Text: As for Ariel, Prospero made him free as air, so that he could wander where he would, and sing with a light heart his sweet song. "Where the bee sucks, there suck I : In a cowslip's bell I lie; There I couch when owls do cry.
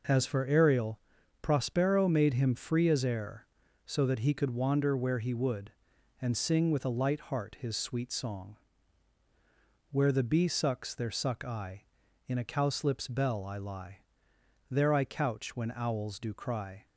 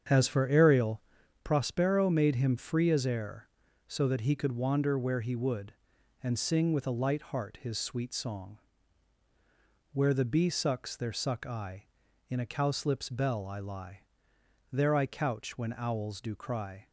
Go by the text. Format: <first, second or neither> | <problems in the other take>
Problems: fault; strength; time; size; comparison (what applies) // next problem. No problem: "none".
first | starts louder than the rest; strong; until 1.5 s; 7.5 dB